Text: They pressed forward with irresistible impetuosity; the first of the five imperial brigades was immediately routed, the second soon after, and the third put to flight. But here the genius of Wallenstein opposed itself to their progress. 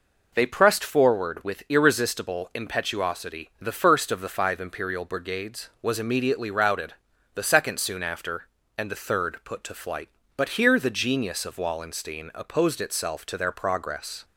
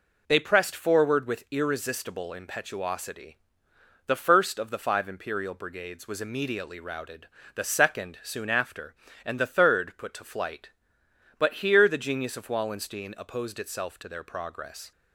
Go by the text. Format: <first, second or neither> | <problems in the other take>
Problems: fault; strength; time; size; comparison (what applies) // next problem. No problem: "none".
neither | none